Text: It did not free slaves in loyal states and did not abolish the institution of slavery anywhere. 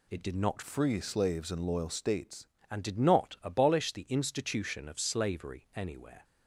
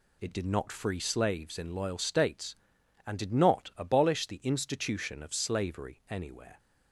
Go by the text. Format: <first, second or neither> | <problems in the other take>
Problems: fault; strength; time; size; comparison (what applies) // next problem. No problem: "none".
second | changes voice from "free" to "states"; from 0.6 to 2.4 s; 1.8 s long